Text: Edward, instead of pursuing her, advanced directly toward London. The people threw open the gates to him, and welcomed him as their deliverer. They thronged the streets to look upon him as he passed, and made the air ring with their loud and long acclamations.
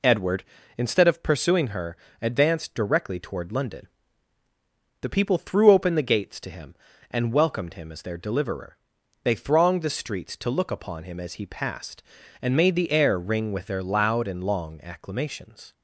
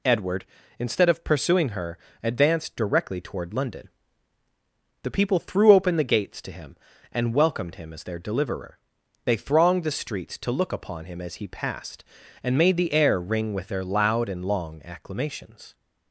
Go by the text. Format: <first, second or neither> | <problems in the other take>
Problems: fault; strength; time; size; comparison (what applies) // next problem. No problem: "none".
second | starts louder than the rest; until 1.2 s; 3.5 dB